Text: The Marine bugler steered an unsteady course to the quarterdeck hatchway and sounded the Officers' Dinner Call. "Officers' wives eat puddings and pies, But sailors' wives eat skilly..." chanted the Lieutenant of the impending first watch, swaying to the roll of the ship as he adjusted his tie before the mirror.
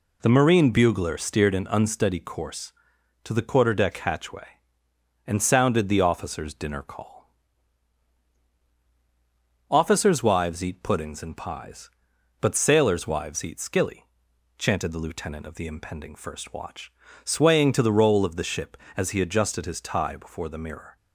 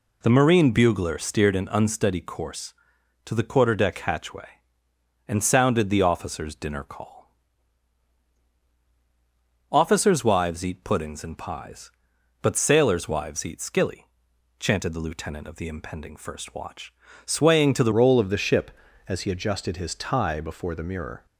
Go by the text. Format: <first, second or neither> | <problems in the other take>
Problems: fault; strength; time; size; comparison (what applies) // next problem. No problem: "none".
first | changes voice at "roll"; from 17.9 s on; 3.3 s long